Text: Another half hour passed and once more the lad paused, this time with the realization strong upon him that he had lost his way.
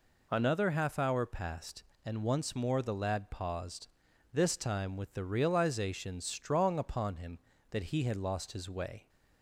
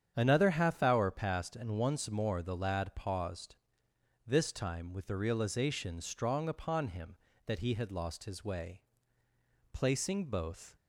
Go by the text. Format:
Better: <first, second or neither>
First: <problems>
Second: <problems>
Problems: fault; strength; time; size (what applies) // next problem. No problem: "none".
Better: first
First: none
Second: starts louder than the rest; strong; until 1.1 s; 8.5 dB // goes on to say "Placing both"; noticeable; from 9.7 s on; 1.0 s long